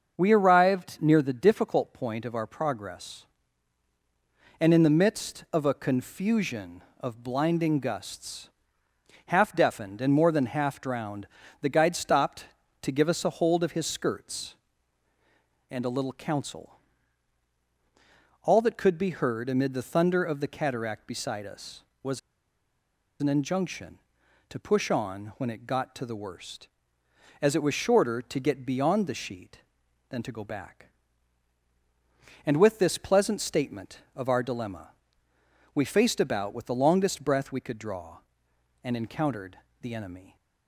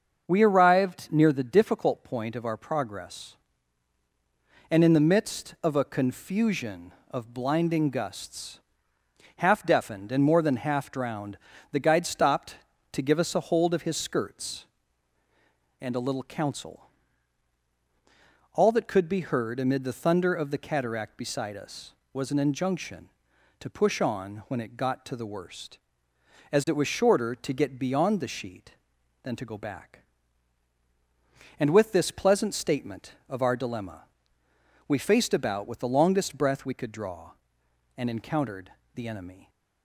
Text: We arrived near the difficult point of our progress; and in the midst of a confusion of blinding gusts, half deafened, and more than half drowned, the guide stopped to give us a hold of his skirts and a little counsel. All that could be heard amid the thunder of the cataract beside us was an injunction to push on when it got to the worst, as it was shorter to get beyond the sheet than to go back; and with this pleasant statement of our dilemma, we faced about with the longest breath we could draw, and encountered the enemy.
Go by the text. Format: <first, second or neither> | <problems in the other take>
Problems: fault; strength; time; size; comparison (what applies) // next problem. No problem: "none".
second | starts louder than the rest; until 1.2 s; 6.5 dB; also in the second // pauses between "was" and "an"; at 22.1 s; 1.0 s long // pauses between "encountered" and "the"; slight; at 39.5 s; 0.22 s long; slight in the second